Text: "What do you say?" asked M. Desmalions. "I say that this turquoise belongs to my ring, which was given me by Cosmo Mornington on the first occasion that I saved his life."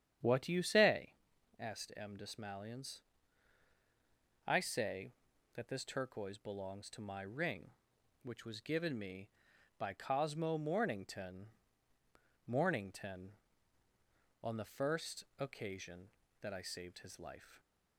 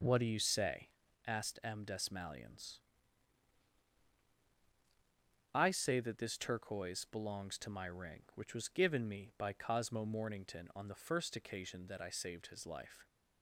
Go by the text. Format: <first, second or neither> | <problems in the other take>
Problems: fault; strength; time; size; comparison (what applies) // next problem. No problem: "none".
second | starts louder than the rest; strong; until 1.6 s; 9.5 dB // says "Mornington" twice; at 12.4 s // pauses between "first" and "occasion"; slight; at 15.2 s; 0.16 s long